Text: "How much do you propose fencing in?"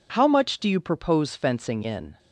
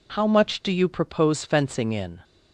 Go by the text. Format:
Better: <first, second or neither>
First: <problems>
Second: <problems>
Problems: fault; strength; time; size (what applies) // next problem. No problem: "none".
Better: neither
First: none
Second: none